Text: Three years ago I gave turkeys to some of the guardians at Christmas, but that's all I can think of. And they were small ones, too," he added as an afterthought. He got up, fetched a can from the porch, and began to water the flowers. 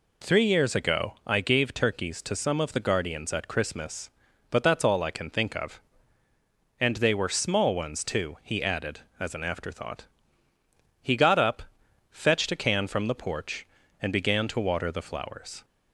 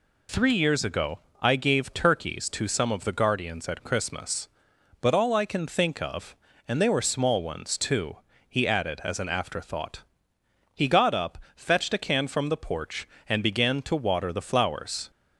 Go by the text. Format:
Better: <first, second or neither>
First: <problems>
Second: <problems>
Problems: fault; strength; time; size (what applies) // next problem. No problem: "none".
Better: first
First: none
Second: pauses between "ago" and "I"; slight; at 1.1 s; 0.24 s long // skips "that's"; at 5.1 s